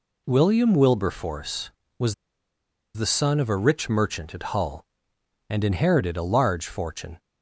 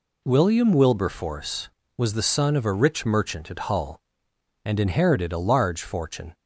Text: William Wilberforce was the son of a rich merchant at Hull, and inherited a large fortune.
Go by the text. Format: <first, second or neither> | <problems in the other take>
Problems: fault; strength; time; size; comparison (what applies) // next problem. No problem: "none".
second | pauses between "was" and "the"; noticeable; at 2.1 s; 0.80 s long